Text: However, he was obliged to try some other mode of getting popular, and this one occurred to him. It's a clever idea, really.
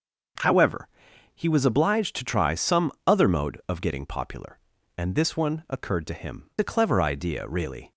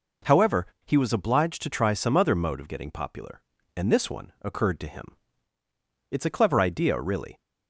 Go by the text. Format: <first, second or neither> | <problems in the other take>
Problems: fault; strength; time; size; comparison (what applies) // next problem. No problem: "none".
second | starts louder than the rest; until 1.8 s; 6.5 dB // pauses between "some" and "other"; slight; at 2.9 s; 0.16 s long // skips "It's"; at 6.5 s